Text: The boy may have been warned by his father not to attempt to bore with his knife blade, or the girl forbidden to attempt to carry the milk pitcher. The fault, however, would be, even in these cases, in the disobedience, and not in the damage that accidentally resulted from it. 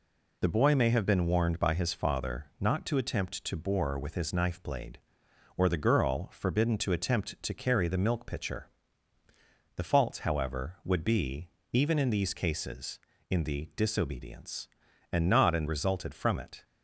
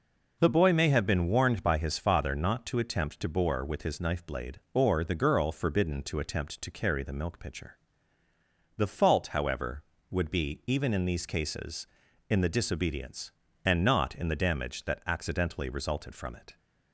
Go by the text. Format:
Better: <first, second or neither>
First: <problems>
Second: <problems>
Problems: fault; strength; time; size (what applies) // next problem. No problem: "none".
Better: second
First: skips "the damage that accidentally"; at 15.6 s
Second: none